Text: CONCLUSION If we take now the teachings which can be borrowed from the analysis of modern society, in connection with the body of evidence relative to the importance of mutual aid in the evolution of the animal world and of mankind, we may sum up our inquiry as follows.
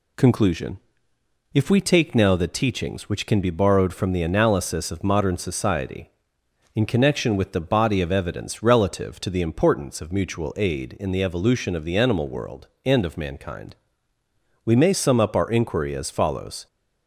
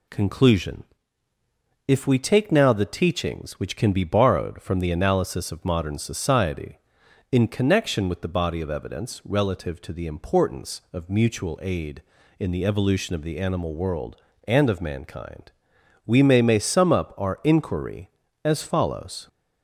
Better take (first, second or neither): first